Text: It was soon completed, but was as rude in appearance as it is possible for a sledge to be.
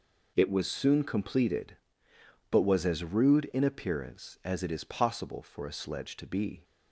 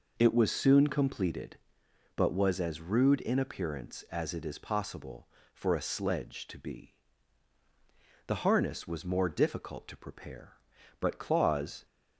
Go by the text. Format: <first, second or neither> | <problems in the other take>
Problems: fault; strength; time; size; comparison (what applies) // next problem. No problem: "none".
first | goes on to say "The harness was more difficult to prepare but Claus"; strong; from 8.2 s on; 3.6 s long